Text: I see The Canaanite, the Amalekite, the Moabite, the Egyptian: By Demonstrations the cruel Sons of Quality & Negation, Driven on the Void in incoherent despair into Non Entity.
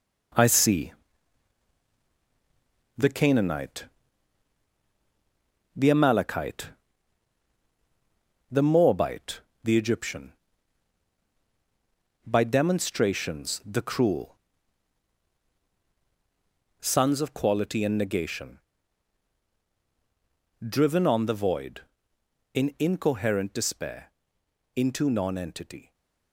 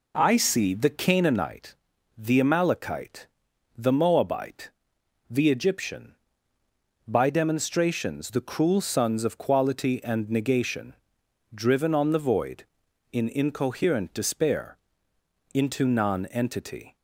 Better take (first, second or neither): second